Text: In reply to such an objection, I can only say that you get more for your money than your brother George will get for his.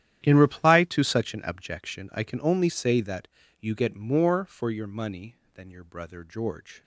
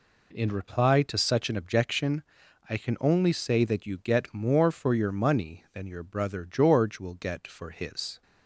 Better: second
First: starts louder than the rest; strong; until 1.2 s; 11 dB // pauses between "that" and "you"; slight; at 3.2 s; 0.32 s long // stops before "will get for his"; at 6.8 s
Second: none

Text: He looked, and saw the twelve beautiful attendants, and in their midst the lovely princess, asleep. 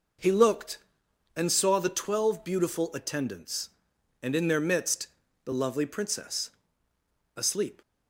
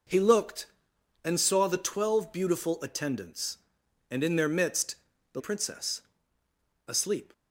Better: first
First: pauses between "midst" and "the"; at 5.0 s; 0.38 s long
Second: pauses between "midst" and "the"; at 4.9 s; 0.38 s long // skips "lovely"; at 5.3 s

